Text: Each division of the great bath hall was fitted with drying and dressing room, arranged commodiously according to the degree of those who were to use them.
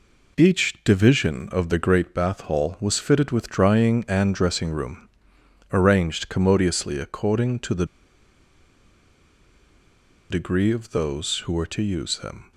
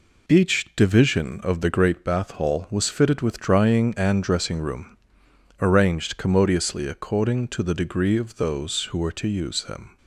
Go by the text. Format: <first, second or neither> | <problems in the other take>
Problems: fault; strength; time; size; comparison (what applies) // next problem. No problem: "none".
second | pauses between "the" and "degree"; strong; at 7.8 s; 2.4 s long